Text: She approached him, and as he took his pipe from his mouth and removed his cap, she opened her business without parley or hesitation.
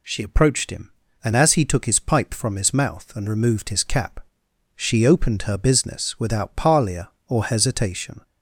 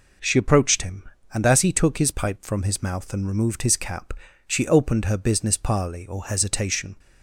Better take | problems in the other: first | skips "without"; at 5.5 s

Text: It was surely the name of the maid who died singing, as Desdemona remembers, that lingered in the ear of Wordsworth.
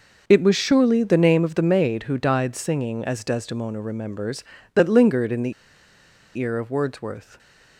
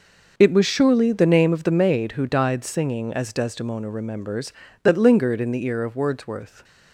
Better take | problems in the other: second | pauses between "the" and "ear"; noticeable; at 5.5 s; 0.85 s long

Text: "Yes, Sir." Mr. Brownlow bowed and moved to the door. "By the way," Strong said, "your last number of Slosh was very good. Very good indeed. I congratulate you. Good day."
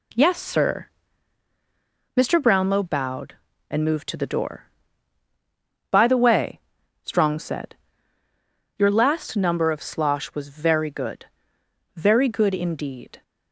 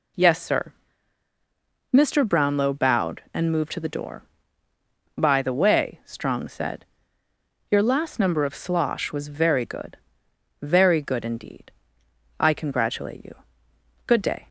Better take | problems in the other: second | stops before "I congratulate you Good day"; at 13.2 s

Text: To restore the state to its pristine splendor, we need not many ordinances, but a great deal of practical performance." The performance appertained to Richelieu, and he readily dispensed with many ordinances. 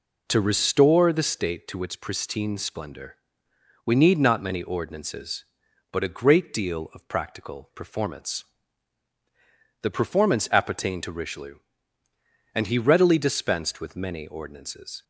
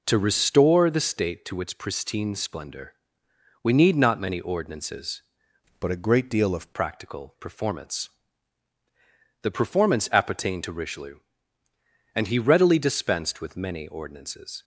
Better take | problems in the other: first | changes voice from "but" to "of"; from 5.7 to 6.7 s; 1.0 s long

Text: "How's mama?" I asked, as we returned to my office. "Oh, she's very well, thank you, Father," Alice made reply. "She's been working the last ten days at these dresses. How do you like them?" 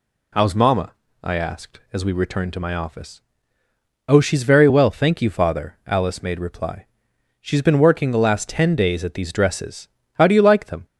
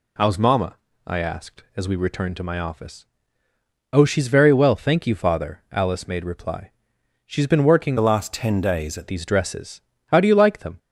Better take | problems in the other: first | changes voice from "the" to "at"; from 7.9 to 9.0 s; 1.1 s long

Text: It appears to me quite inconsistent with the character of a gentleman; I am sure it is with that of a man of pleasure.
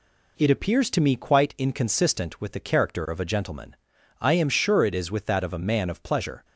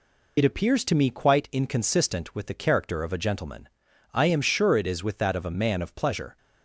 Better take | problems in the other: first | loses the start of "It"; at 0.3 s; 60 ms

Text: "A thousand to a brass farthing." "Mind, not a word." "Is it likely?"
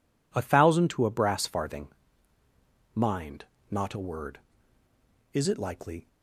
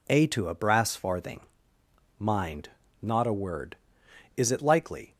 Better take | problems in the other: first | skips "thousand"; at 0.2 s

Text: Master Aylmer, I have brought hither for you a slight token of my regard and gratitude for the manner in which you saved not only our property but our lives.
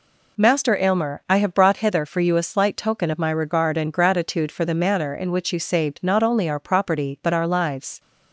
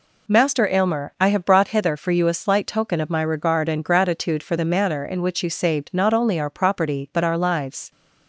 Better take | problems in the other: neither | none

